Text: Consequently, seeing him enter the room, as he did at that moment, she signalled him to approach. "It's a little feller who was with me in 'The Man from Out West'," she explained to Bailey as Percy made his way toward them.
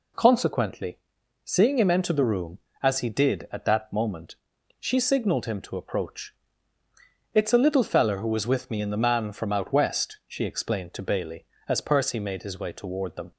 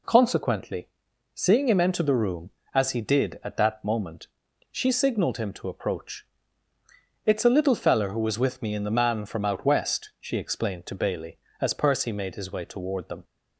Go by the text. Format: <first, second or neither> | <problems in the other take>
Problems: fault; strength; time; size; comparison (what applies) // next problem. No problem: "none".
neither | none